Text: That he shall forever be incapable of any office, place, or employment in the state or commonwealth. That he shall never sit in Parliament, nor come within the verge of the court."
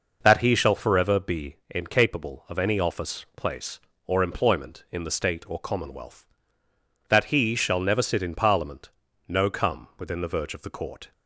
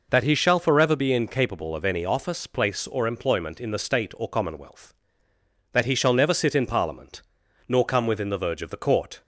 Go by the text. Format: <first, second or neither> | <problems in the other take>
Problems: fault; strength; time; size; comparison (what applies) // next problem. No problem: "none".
second | says "no" for "nor"; at 9.2 s